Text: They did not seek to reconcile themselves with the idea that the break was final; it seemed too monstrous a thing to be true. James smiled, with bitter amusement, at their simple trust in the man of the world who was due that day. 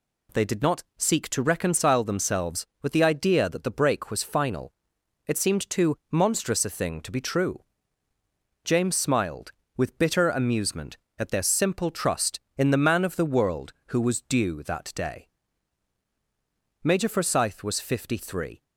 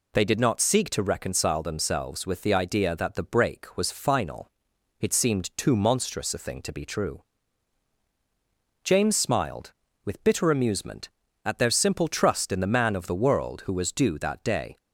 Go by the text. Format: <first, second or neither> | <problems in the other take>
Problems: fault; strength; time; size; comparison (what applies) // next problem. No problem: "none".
second | pauses between "too" and "monstrous"; slight; at 5.9 s; 0.16 s long // goes on to say "Major Forsyth was fifty three"; strong; from 16.8 s on; 1.7 s long